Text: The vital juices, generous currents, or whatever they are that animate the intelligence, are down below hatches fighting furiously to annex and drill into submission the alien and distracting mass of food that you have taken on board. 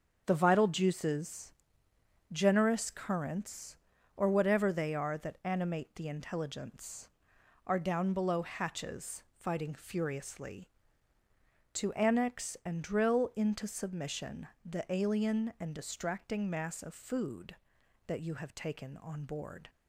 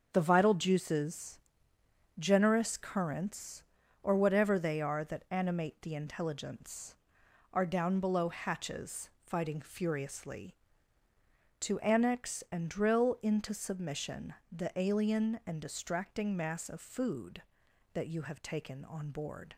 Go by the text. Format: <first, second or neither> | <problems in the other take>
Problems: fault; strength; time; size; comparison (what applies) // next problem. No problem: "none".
neither | starts louder than the rest; the same in both // pauses between "hatches" and "fighting"; slight; the same in both // pauses between "submission" and "the"; slight; the same in both